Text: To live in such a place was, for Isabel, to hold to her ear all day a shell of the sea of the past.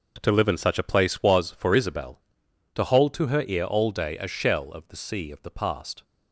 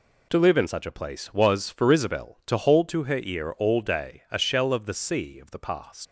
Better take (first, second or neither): first